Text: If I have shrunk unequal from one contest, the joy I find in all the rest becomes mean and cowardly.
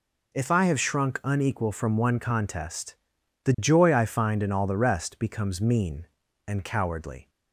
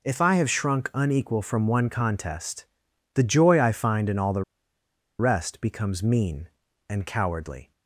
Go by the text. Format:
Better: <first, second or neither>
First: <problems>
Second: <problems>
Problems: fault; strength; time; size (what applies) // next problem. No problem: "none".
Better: first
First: none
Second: pauses between "the" and "rest"; noticeable; at 4.4 s; 0.77 s long